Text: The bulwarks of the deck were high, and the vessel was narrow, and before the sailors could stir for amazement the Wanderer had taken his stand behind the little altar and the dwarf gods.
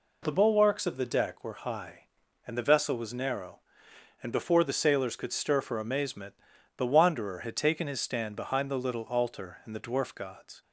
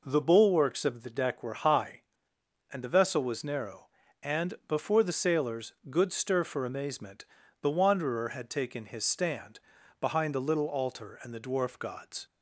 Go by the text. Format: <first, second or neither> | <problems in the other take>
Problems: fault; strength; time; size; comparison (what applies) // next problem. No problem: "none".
first | says "good" for "could"; at 5.9 s // pauses between "amazement" and "the"; at 7.2 s; 0.38 s long; noticeable in the first // pauses between "stand" and "behind"; at 9.5 s; 0.40 s long